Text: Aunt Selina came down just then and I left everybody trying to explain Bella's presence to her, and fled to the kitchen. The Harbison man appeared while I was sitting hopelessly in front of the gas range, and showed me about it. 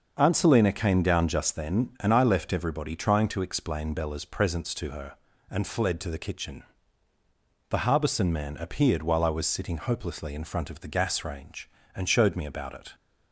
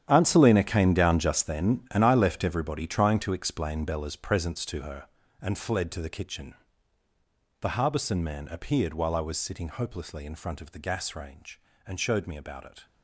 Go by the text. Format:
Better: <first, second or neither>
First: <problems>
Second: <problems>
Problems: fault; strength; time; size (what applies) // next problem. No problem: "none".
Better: first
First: starts louder than the rest; until 1.1 s; 6.5 dB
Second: gets quieter; strong; throughout; 13.5 dB // starts louder than the rest; strong; until 1.0 s; 10 dB